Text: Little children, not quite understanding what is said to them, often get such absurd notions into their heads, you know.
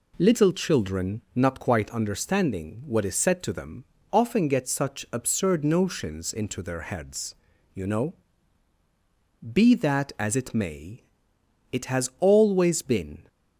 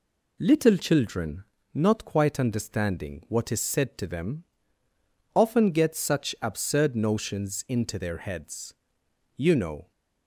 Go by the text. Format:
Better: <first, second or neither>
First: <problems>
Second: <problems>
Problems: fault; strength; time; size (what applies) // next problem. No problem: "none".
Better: second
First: goes on to say "Be that as it may it has always been"; strong; from 9.5 s on; 3.7 s long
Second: none